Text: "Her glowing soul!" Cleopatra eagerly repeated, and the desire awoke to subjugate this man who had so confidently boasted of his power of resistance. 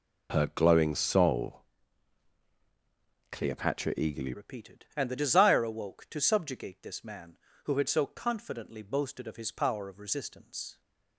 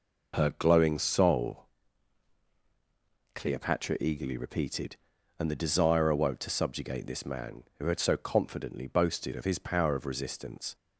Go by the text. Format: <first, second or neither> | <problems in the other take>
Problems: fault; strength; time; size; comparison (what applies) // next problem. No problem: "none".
second | changes voice at "repeated"; from 4.3 s on; 6.5 s long